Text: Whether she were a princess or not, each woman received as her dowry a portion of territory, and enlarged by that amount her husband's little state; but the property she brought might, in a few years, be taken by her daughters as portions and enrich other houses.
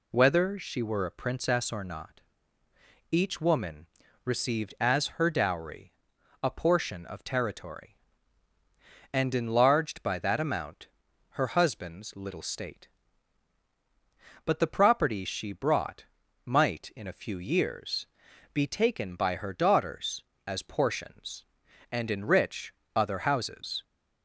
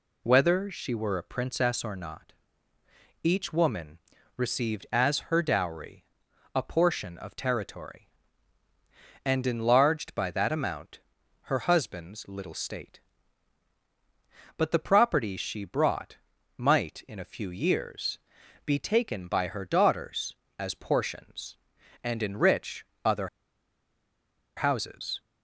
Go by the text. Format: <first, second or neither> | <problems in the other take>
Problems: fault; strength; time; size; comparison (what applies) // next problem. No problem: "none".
first | pauses between "woman" and "received"; at 3.9 s; 0.38 s long; also in the first // pauses between "dowry" and "a"; noticeable; at 6.0 s; 0.50 s long; noticeable in the first // pauses between "amount" and "her"; at 10.9 s; 0.42 s long; also in the first // pauses between "brought" and "might"; at 16.1 s; 0.38 s long; also in the first // pauses between "enrich" and "other"; slight; at 22.8 s; 0.18 s long; slight in the first // pauses between "other" and "houses"; strong; at 23.2 s; 1.2 s long